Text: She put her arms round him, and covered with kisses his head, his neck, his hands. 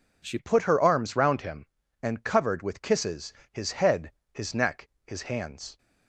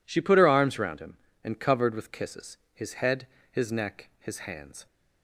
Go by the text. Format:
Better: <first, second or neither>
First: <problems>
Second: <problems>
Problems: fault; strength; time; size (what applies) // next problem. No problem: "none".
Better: second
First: changes voice at "put"; from 0.3 s on; 5.4 s long // pauses between "kisses" and "his"; slight; at 3.3 s; 0.18 s long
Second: pauses between "kisses" and "his"; slight; at 2.5 s; 0.18 s long